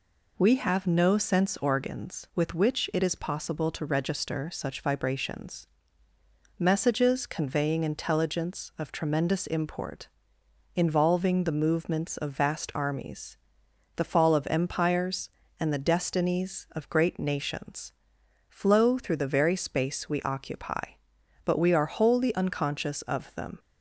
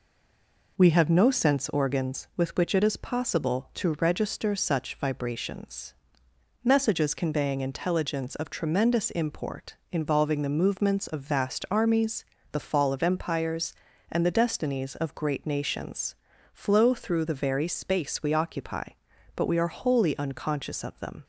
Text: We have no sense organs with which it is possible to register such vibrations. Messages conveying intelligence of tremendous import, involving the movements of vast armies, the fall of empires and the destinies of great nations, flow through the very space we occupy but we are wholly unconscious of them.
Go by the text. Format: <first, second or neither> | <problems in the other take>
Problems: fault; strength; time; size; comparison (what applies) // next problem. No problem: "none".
first | stays silent before the first word; slight; until 0.7 s; 0.7 s long